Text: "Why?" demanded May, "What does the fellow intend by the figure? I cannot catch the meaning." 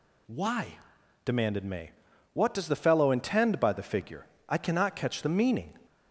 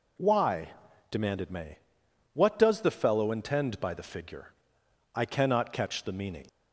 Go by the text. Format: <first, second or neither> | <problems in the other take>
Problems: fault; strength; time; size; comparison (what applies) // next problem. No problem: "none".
neither | none